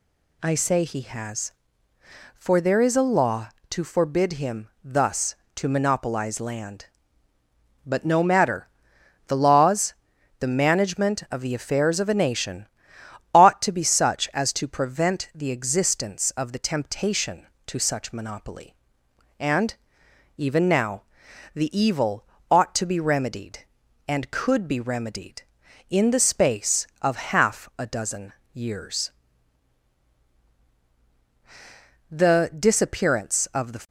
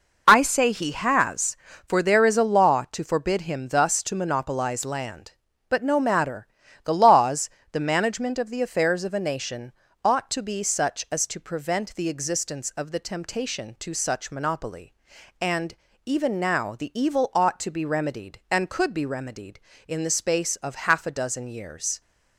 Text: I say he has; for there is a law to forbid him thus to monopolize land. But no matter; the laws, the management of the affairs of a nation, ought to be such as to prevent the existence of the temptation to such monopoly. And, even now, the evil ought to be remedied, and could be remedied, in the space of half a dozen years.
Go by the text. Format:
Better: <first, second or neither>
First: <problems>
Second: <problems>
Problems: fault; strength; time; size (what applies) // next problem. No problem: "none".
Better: second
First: pauses between "evil" and "ought"; slight; at 22.2 s; 0.24 s long // pauses between "dozen" and "years"; slight; at 28.3 s; 0.22 s long // goes on to say "The disappearance of the"; strong; from 32.1 s on; 1.7 s long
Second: none